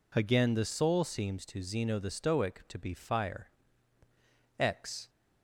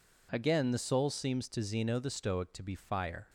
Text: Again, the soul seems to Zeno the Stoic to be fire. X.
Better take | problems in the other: first | stops before "X"; at 3.2 s

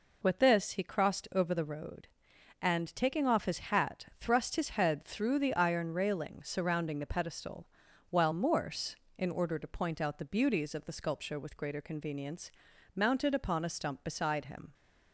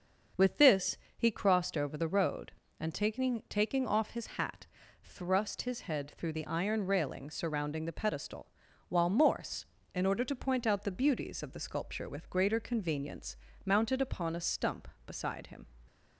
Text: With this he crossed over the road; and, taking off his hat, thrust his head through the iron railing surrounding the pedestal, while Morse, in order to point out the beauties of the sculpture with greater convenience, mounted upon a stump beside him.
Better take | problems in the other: first | starts louder than the rest; until 1.5 s; 6.5 dB // pauses between "this" and "he"; slight; at 0.9 s; 0.20 s long // says "taking" twice; at 3.4 s

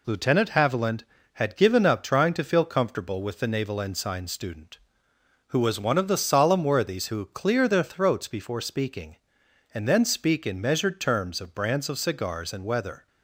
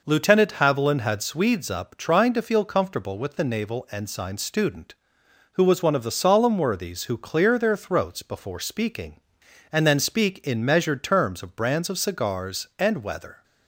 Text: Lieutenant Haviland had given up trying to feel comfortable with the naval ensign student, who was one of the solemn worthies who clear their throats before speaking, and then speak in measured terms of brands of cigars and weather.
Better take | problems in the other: first | says "swedes" for "given"; at 1.2 s

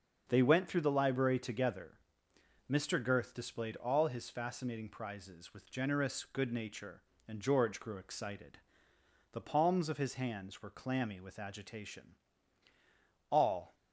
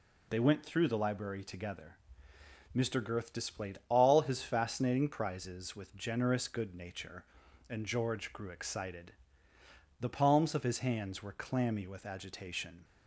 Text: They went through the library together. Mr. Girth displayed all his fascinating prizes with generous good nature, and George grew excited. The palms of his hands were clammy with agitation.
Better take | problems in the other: second | starts louder than the rest; until 1.2 s; 6 dB // goes on to say "All"; slight; from 13.2 s on; 0.44 s long

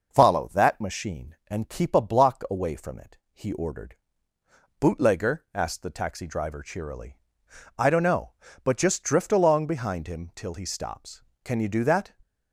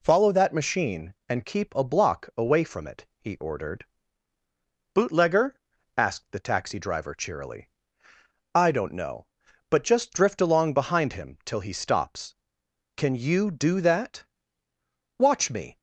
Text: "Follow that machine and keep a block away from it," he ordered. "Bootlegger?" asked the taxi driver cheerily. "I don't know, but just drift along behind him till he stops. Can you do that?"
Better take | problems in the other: first | goes on to say "Watch me"; from 15.1 s on; 0.58 s long

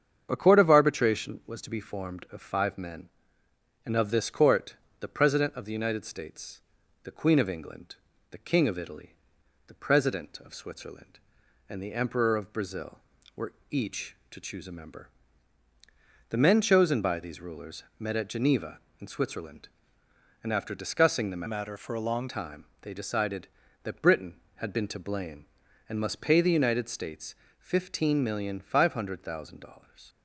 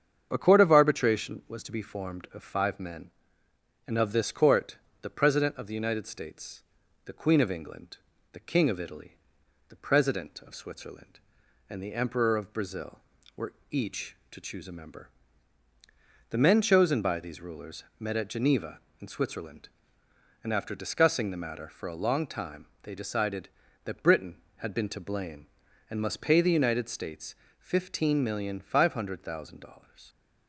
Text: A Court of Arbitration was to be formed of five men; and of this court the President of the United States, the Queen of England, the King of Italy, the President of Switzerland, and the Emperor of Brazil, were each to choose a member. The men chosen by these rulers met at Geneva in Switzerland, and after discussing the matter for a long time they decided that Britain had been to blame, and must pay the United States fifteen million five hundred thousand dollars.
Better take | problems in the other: second | starts louder than the rest; strong; until 1.3 s; 8 dB; strong in the second // pauses between "court" and "the"; slight; at 4.7 s; 0.24 s long; slight in the second // pauses between "were" and "each"; slight; at 13.5 s; 0.18 s long; slight in the second // pauses between "rulers" and "met"; slight; at 17.8 s; 0.16 s long; slight in the second // changes voice from "matter" to "long"; from 21.4 to 22.2 s; 0.8 s long // pauses between "time" and "they"; slight; at 22.6 s; 0.18 s long; slight in the second // pauses between "States" and "fifteen"; slight; at 27.3 s; 0.24 s long; slight in the second

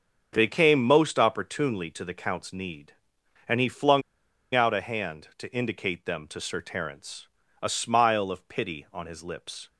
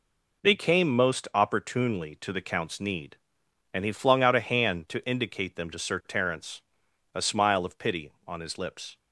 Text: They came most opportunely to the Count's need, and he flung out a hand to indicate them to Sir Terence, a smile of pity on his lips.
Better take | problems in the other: second | starts louder than the rest; until 1.3 s; 6 dB // pauses between "flung" and "out"; noticeable; at 4.0 s; 0.52 s long

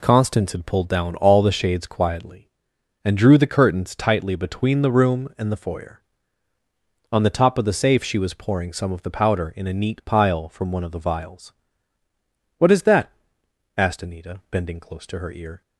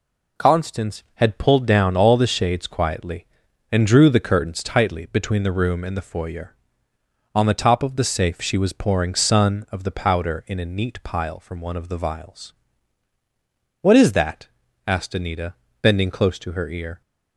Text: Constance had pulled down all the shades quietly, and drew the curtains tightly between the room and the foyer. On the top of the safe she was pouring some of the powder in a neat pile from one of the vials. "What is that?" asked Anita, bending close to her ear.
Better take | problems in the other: first | says "sun" for "some"; at 9.1 s

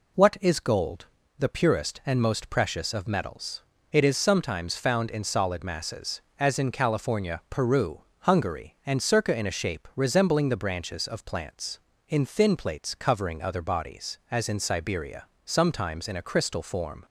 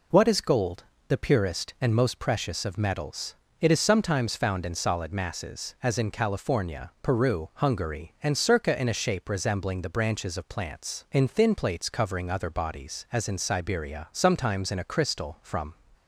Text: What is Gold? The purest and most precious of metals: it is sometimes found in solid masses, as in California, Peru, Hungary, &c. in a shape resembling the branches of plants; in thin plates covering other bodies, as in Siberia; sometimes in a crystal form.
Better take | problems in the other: first | says "from" for "form"; at 15.4 s

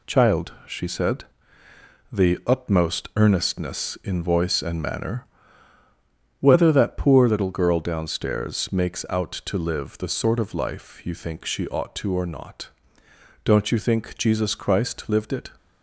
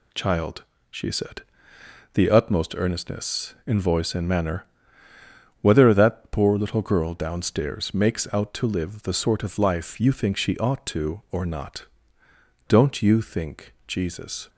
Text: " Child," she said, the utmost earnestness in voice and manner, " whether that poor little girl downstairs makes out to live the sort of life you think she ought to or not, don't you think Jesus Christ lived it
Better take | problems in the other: first | stops before "Christ lived it"; at 14.4 s

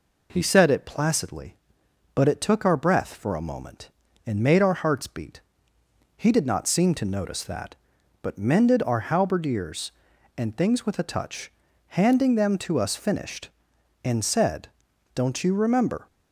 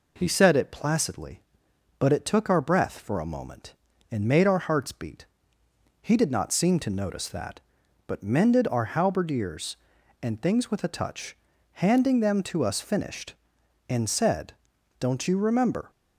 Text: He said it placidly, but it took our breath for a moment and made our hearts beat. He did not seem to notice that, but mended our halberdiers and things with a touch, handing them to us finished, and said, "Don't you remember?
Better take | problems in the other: neither | none

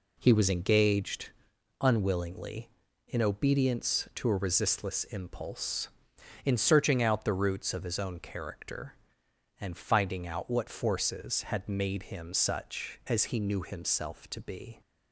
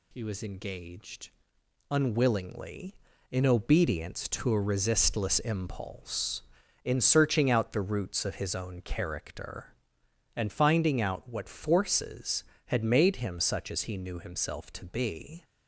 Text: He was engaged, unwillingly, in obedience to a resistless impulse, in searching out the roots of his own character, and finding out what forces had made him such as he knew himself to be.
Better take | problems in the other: neither | none

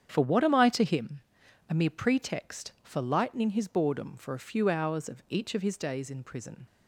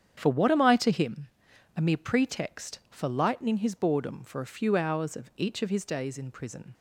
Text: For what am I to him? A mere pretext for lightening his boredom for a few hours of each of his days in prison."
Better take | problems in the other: neither | starts louder than the rest; strong; the same in both

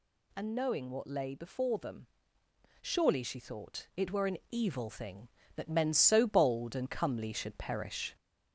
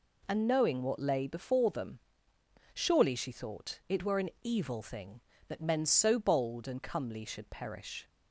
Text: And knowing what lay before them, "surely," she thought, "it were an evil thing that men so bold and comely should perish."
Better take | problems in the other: second | gets louder; slight; throughout; 2.5 dB

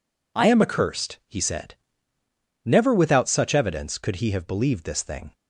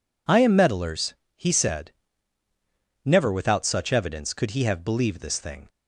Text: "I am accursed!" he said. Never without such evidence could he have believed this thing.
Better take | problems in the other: first | says "meddlers" for "accursed"; at 0.5 s

